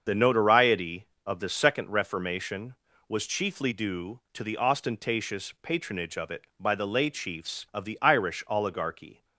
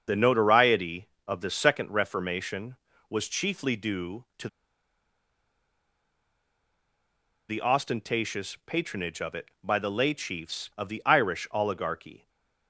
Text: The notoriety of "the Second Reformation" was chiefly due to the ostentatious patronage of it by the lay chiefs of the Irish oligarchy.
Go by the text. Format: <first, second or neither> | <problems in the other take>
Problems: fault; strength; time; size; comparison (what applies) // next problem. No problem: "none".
first | starts louder than the rest; until 1.2 s; 7 dB; also in the first // pauses between "to" and "the"; strong; at 4.4 s; 3.0 s long // stays silent after the last word; slight; from 12.1 s on; 0.5 s long